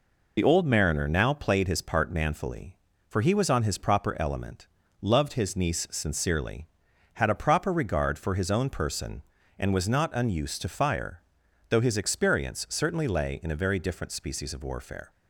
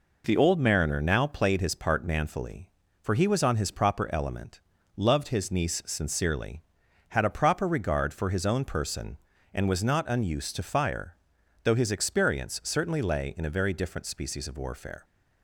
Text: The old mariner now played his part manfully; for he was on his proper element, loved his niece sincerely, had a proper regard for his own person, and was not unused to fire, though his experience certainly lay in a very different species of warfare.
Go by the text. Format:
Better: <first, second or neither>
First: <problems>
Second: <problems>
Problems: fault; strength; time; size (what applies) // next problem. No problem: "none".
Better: second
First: loses the start of "The"; at 0.3 s; 60 ms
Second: none